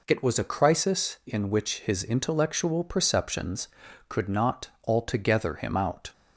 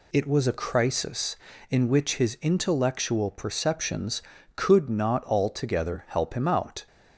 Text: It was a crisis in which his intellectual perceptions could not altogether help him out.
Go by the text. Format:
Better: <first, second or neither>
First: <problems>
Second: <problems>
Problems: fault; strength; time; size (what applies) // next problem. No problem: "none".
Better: second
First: pauses between "not" and "altogether"; slight; at 4.6 s; 0.18 s long // skips "help"; at 5.5 s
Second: none